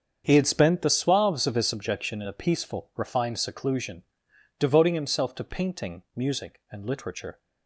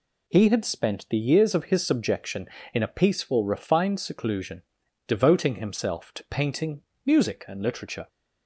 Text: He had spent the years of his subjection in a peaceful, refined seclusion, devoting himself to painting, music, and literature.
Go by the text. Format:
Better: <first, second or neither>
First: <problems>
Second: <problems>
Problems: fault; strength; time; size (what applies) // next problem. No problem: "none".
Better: second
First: starts louder than the rest; strong; until 1.2 s; 7 dB // says "suaves" for "years"; at 0.8 s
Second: none